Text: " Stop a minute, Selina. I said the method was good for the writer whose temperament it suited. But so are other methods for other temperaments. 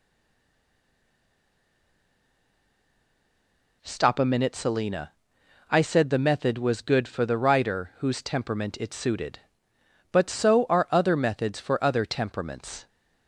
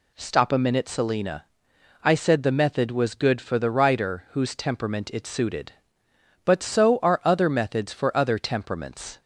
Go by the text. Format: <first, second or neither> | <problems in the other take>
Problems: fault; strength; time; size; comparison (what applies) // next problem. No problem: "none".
second | stays silent before the first word; strong; until 3.8 s; 3.8 s long